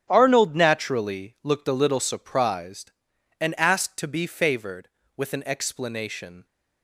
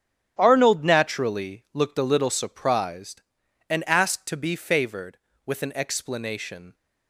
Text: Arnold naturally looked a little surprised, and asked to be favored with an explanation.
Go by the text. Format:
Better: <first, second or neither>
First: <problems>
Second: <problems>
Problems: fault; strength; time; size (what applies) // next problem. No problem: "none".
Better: neither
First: starts louder than the rest; strong; until 1.1 s; 10.5 dB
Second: starts louder than the rest; strong; until 1.4 s; 10.5 dB